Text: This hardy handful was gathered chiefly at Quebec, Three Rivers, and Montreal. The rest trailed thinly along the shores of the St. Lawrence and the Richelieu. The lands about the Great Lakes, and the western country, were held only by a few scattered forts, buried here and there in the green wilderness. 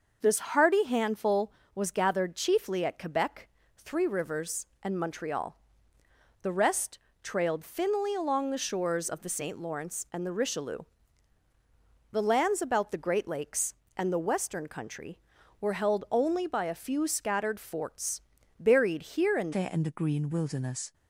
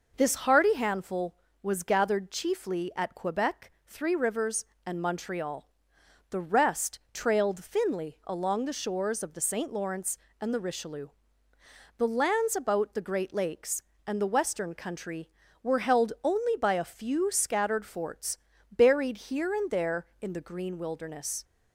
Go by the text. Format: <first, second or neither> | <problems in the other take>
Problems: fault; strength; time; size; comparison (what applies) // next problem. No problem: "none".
second | pauses between "rest" and "trailed"; slight; at 6.9 s; 0.24 s long // changes voice at "there"; from 19.5 s on; 1.4 s long